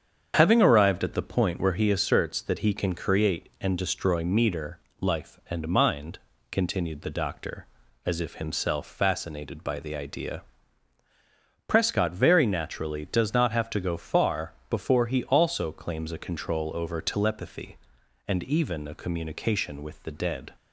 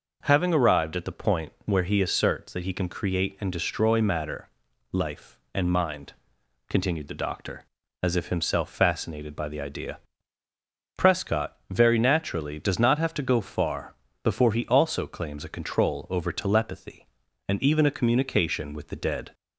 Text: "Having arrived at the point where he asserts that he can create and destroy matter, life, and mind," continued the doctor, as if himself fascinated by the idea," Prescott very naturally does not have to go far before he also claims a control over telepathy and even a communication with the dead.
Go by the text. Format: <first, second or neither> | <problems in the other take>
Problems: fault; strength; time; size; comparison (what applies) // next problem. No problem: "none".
second | starts louder than the rest; strong; until 1.3 s; 7.5 dB // says "meter" for "matter"; at 4.2 s // pauses between "far" and "before"; slight; at 14.5 s; 0.18 s long; slight in the second